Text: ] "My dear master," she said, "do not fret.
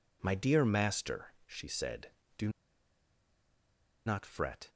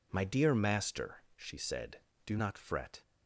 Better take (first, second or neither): second